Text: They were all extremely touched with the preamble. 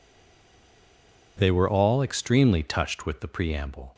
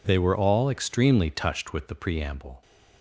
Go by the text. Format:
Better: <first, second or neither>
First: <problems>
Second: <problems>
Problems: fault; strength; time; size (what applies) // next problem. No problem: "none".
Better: second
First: stays silent before the first word; noticeable; until 1.3 s; 1.3 s long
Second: none